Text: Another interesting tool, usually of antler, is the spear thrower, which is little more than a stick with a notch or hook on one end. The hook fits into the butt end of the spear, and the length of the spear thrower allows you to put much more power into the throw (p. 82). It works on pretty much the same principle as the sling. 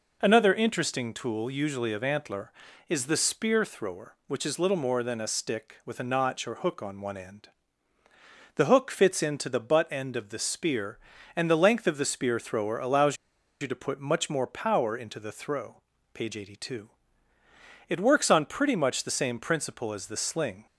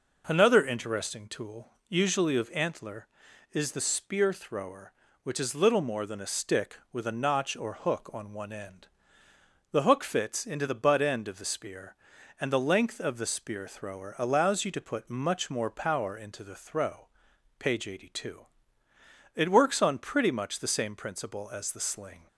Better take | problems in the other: second | pauses between "allows" and "you"; at 13.1 s; 0.45 s long

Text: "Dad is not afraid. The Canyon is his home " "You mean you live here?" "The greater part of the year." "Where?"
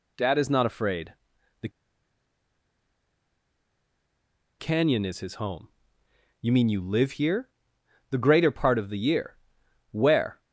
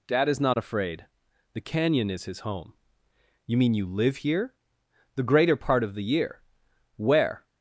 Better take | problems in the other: second | pauses between "The" and "Canyon"; strong; at 1.6 s; 2.9 s long

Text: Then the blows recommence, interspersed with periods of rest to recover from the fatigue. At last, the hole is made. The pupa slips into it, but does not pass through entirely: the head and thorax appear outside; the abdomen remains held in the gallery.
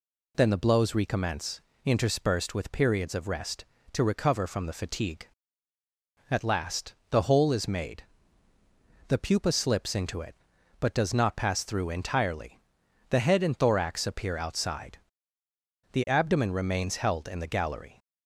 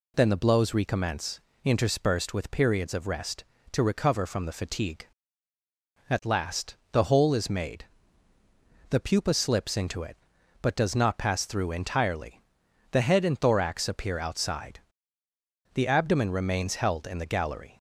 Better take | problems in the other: neither | none

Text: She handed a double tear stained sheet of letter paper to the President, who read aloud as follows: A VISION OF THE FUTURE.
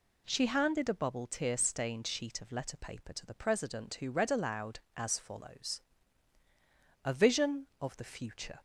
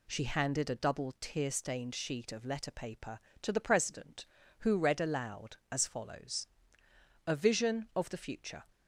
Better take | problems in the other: second | says "bubble" for "double"; at 0.9 s

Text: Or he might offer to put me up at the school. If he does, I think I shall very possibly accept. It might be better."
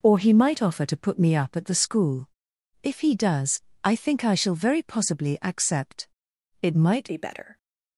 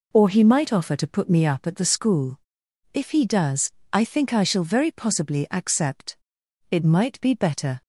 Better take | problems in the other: second | changes voice at "be"; from 7.0 s on; 0.5 s long

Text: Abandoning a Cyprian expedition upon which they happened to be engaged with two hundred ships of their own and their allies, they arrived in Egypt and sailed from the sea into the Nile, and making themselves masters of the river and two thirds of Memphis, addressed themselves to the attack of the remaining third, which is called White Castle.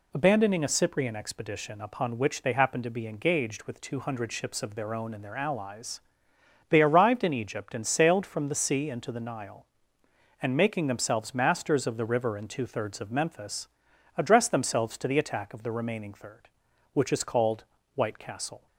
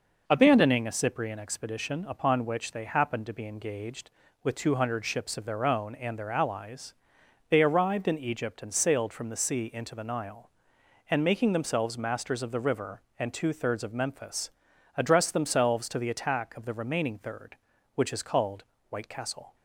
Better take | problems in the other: neither | pauses between "called" and "White"; slight; the same in both

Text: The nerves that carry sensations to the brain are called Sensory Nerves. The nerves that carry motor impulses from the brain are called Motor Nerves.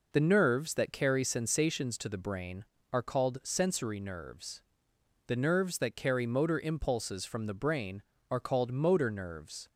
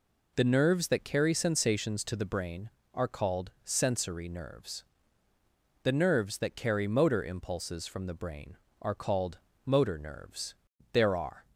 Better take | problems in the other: first | pauses between "called" and "Motor"; slight; at 9.3 s; 0.26 s long // goes on to say "There are"; from 10.9 s on; 0.50 s long

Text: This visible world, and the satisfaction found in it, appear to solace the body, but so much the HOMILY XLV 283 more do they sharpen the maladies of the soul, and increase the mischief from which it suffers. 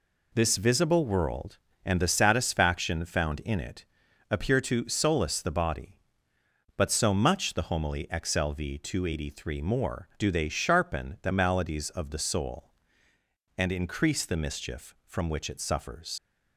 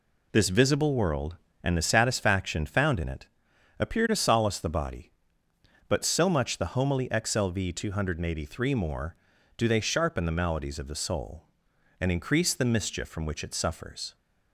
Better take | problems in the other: second | leaves "suffers" unfinished; at 16.1 s; 60 ms

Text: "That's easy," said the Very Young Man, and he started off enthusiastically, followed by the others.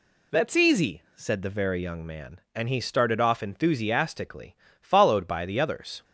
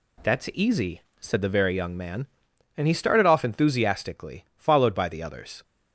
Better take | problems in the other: neither | none

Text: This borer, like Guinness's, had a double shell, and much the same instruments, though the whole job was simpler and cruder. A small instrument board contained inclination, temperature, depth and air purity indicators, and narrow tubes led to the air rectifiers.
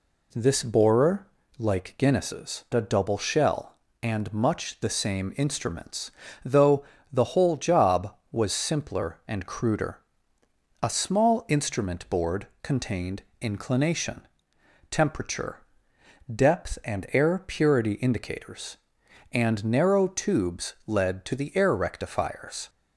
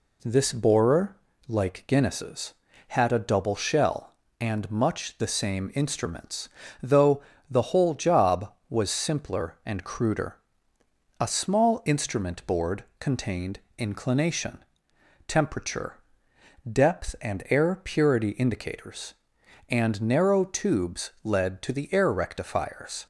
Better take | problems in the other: second | skips "had"; at 2.6 s // pauses between "though" and "the"; slight; at 6.8 s; 0.26 s long; slight in the second // pauses between "contained" and "inclination"; slight; at 13.2 s; 0.18 s long; slight in the second

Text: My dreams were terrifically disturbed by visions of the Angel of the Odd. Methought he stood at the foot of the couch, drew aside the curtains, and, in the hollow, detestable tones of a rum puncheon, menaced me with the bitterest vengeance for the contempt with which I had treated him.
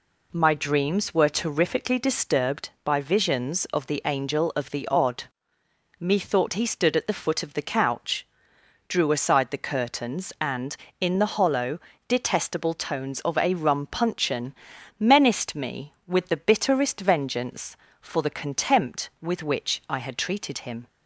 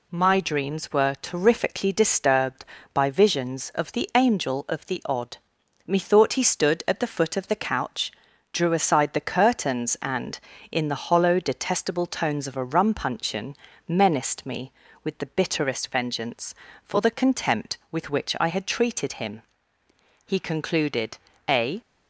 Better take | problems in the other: first | goes on to say "He concluded a"; from 20.2 s on; 1.5 s long

